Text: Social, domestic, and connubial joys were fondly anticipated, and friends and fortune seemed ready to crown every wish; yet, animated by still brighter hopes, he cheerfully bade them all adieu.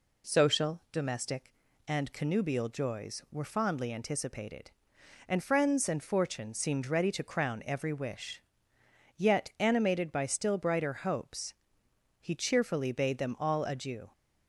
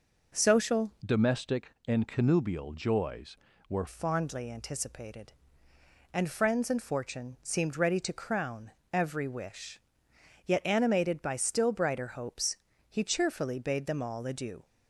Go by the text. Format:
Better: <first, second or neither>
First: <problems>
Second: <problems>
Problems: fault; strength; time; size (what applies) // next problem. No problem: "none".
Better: first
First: none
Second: changes voice from "domestic" to "were"; from 1.0 to 3.8 s; 2.8 s long // pauses between "crown" and "every"; slight; at 8.7 s; 0.22 s long